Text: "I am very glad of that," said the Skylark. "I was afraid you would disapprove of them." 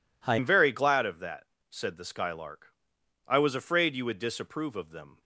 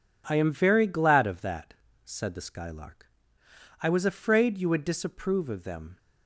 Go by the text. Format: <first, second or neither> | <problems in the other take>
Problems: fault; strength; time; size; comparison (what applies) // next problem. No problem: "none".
second | changes voice at "am"; from 0.3 s on; 4.9 s long